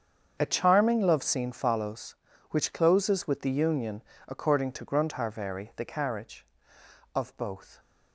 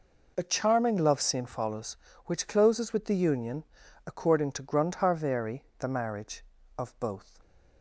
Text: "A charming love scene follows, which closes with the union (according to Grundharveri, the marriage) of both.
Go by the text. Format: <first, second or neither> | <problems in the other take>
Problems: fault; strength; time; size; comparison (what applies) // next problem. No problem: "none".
second | starts louder than the rest; strong; until 1.4 s; 7.5 dB // says "carriage" for "marriage"; at 5.8 s